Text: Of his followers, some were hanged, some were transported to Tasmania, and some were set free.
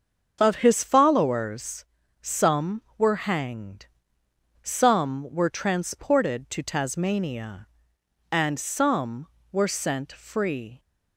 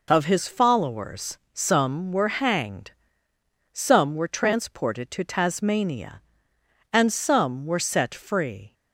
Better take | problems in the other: second | starts louder than the rest; until 1.4 s; 6.5 dB // says "sent" for "set"; at 9.6 s

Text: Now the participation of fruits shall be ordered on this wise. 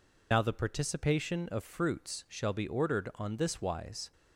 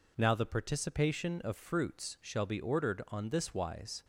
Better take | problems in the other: second | loses the start of "Now"; at 0.3 s; 70 ms

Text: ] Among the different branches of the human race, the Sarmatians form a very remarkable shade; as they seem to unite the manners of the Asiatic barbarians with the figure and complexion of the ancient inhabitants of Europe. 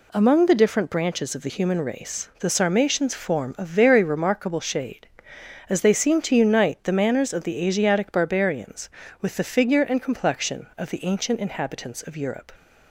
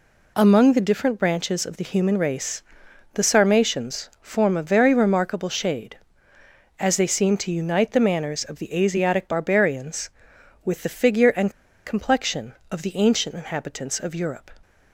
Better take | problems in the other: first | pauses between "and" and "complexion"; slight; at 11.5 s; 0.34 s long

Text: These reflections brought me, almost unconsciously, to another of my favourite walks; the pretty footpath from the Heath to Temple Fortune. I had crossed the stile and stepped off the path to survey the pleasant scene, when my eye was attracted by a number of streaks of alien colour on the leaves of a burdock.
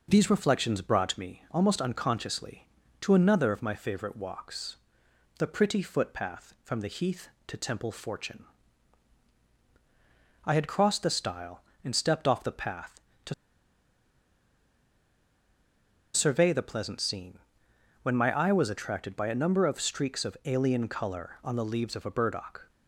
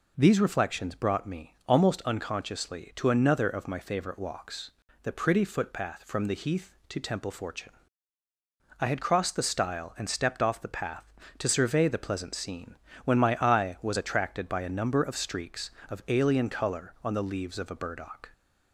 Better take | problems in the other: second | pauses between "to" and "survey"; strong; at 13.3 s; 2.8 s long

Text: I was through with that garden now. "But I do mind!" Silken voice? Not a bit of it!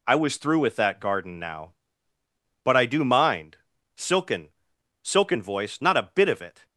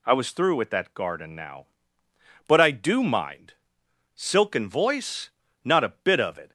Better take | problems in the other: second | says "Silken" twice; at 5.0 s

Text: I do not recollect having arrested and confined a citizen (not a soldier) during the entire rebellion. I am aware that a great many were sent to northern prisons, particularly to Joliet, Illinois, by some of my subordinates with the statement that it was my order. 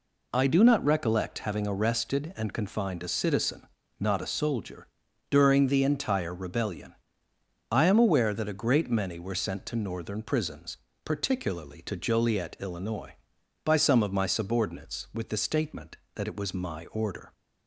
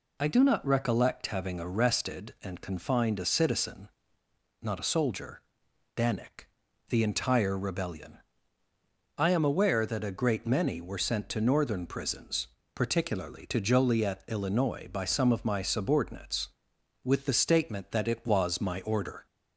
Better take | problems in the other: first | says "danik" for "during"; at 5.9 s

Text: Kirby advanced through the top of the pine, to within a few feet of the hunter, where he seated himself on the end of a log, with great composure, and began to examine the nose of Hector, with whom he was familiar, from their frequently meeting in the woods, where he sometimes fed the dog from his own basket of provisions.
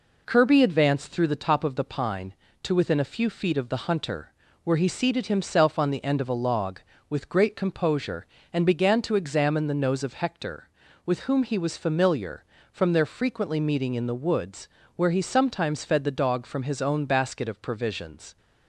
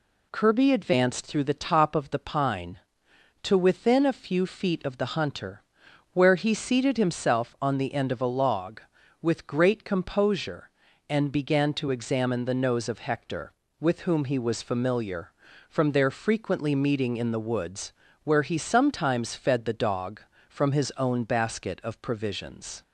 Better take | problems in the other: neither | none

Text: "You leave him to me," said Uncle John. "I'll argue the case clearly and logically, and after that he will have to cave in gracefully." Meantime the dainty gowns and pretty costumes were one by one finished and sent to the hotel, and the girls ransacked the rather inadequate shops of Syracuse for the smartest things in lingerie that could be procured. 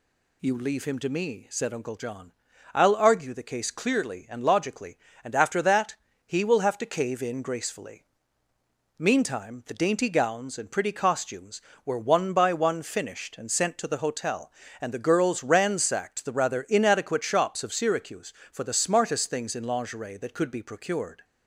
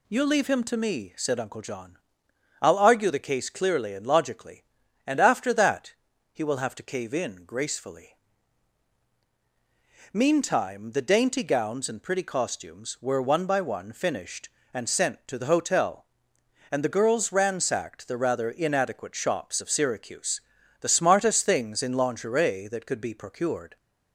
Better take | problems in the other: first | pauses between "that" and "he"; at 5.9 s; 0.40 s long; slight in the first // skips "for"; at 20.5 s

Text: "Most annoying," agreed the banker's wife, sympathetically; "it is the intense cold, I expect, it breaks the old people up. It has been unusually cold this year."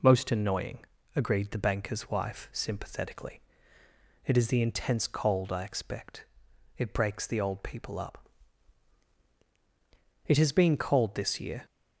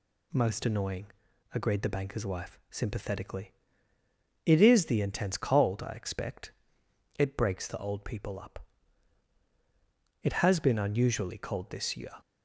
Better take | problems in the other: second | skips "unusually"; at 10.7 s

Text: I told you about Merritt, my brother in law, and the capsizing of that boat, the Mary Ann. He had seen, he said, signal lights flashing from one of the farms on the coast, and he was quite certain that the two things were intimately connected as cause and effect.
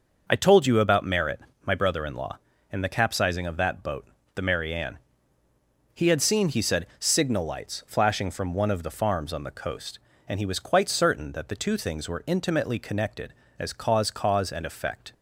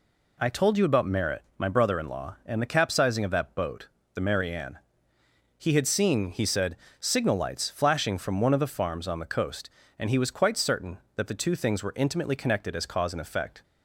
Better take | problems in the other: second | starts louder than the rest; noticeable; until 1.2 s; 6 dB // says "cause" twice; at 14.1 s

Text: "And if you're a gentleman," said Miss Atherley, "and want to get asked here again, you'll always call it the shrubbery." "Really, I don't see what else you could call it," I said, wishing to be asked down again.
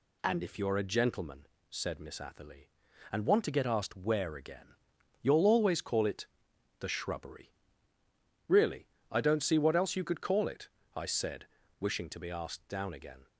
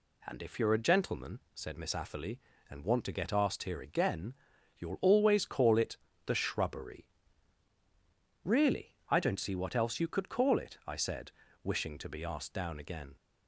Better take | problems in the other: second | says "where" for "here"; at 3.9 s // pauses between "it" and "the"; noticeable; at 6.2 s; 0.54 s long; slight in the second

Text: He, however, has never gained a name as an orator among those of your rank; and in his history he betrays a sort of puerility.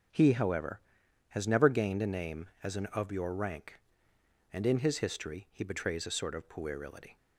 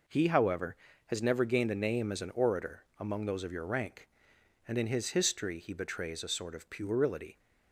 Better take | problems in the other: second | skips "orator among those"; at 2.8 s

